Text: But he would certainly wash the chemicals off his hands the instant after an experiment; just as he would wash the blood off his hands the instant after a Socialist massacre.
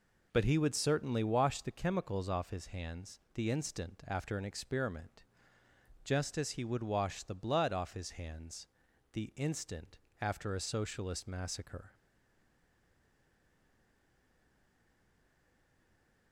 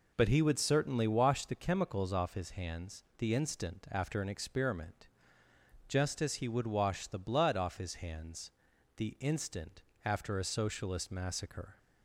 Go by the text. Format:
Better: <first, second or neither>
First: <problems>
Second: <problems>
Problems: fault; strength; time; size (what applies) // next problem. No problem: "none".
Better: second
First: pauses between "hands" and "the"; noticeable; at 8.6 s; 0.46 s long // pauses between "instant" and "after"; slight; at 9.9 s; 0.22 s long // stays silent after the last word; strong; from 11.9 s on; 4.4 s long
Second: pauses between "hands" and "the"; noticeable; at 8.5 s; 0.46 s long // pauses between "instant" and "after"; slight; at 9.8 s; 0.22 s long